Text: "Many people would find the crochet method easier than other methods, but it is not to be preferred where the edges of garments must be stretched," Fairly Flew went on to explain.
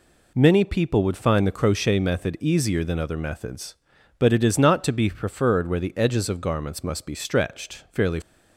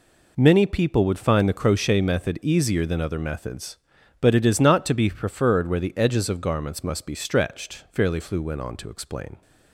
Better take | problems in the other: second | stops before "Flew went on to explain"; at 8.2 s

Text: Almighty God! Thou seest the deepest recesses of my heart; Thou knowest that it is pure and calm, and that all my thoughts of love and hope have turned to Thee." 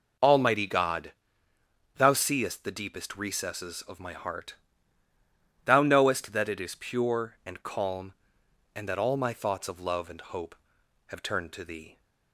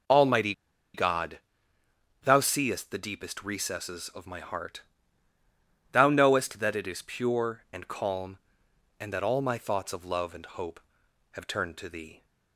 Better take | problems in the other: first | pauses between "Almighty" and "God"; at 0.5 s; 0.41 s long

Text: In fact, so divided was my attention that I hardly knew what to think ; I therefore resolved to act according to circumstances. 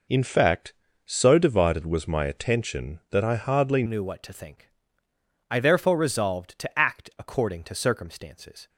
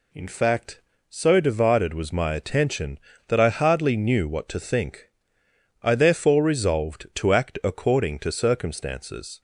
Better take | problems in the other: second | changes voice at "knew"; from 3.8 s on; 4.8 s long

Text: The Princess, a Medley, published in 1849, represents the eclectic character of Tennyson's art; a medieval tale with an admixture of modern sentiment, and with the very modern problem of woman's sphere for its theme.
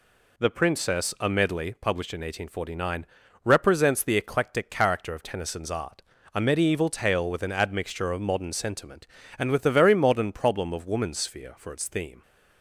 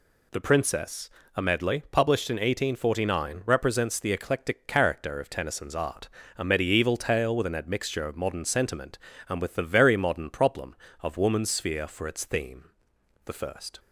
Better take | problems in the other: first | goes on to say "The first"; from 13.2 s on; 0.54 s long

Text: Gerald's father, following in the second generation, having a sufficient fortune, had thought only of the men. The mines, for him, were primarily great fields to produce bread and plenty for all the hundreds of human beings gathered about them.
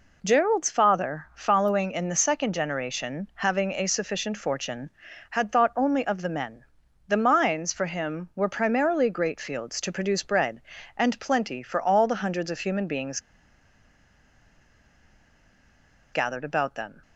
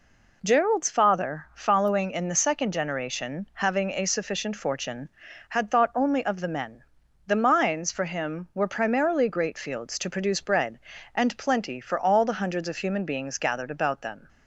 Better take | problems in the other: second | pauses between "beings" and "gathered"; strong; at 13.1 s; 2.9 s long

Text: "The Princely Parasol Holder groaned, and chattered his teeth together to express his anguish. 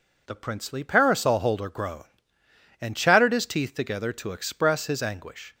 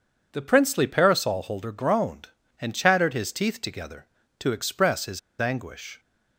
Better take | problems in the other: first | pauses between "his" and "anguish"; slight; at 5.1 s; 0.21 s long

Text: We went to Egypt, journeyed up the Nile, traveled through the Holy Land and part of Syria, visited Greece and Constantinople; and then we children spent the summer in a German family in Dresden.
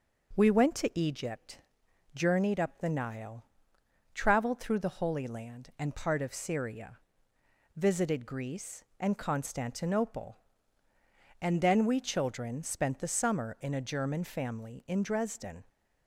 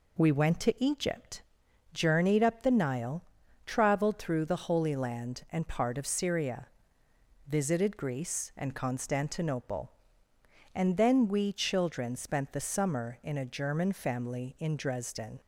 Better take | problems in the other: neither | none

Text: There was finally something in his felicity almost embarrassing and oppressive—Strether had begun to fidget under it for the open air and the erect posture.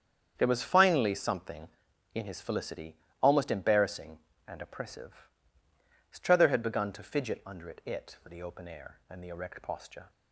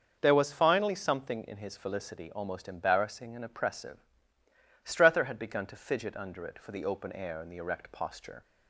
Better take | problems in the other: second | starts louder than the rest; strong; until 1.3 s; 8 dB; also in the second // pauses between "felicity" and "almost"; slight; at 2.9 s; 0.26 s long // says "it" twice; at 7.8 s

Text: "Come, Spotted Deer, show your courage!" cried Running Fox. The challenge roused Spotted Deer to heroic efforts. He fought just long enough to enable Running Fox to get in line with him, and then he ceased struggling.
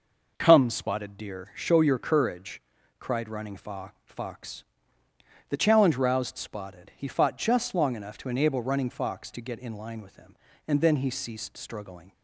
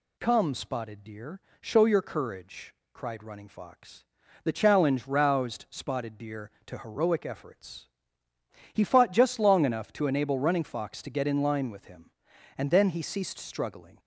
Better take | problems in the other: second | skips "Deer to heroic efforts"; at 6.9 s

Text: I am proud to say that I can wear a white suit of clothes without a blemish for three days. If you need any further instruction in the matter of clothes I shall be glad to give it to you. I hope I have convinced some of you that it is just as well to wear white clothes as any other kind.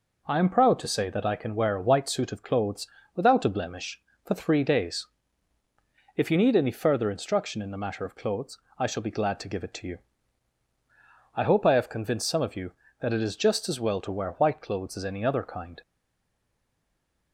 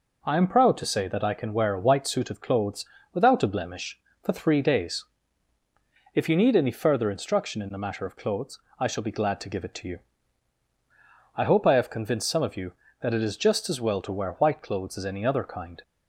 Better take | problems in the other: second | pauses between "clothes" and "without"; slight; at 2.8 s; 0.26 s long; slight in the second // pauses between "clothes" and "I"; slight; at 8.5 s; 0.18 s long; slight in the second // stays silent after the last word; noticeable; from 15.8 s on; 1.5 s long

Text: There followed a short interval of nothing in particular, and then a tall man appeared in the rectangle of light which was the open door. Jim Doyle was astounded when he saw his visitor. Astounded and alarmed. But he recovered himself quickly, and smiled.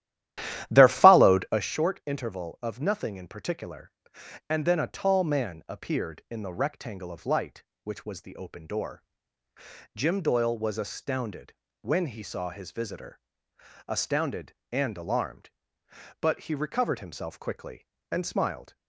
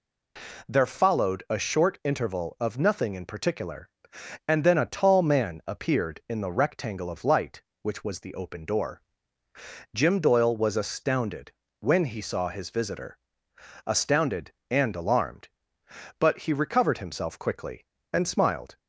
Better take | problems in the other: second | starts louder than the rest; strong; until 1.7 s; 12.5 dB // pauses between "astounded" and "when"; slight; at 11.5 s; 0.28 s long; slight in the second

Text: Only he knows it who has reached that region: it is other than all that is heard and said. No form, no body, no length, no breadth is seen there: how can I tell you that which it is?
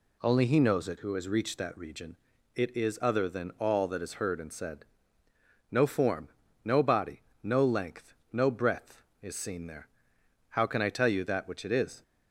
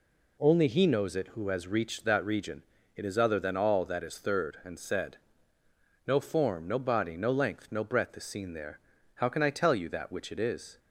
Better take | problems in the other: first | says "third" for "heard"; at 4.1 s

